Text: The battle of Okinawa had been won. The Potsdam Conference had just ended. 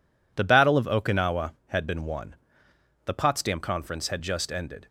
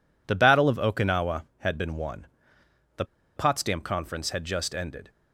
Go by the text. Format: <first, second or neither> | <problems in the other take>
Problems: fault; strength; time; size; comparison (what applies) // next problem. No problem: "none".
first | pauses between "The" and "Potsdam"; slight; at 3.0 s; 0.31 s long